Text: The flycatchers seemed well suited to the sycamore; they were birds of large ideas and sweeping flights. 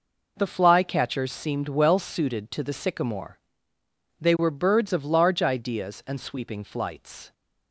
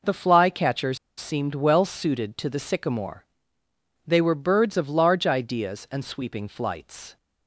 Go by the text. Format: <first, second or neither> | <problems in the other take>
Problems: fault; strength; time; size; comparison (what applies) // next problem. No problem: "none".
first | pauses between "flycatchers" and "seemed"; slight; at 0.9 s; 0.20 s long